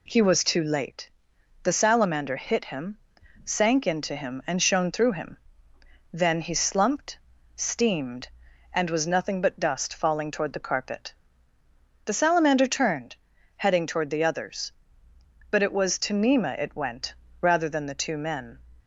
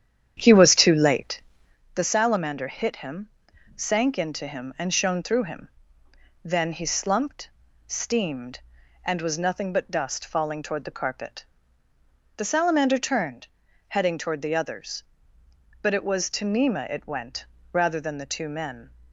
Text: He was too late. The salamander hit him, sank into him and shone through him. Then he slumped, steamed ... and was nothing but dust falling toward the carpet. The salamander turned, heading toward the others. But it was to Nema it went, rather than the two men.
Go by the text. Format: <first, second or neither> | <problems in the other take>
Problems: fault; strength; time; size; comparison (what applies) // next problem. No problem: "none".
first | starts louder than the rest; strong; until 1.8 s; 9.5 dB